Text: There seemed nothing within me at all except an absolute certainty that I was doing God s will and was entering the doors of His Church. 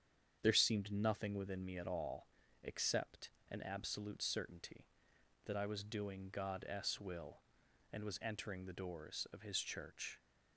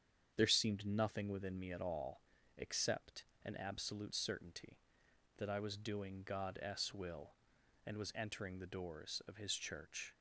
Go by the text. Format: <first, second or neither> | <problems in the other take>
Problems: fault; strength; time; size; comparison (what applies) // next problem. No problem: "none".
neither | starts louder than the rest; strong; the same in both // pauses between "all" and "except"; slight; the same in both // pauses between "except" and "an"; slight; the same in both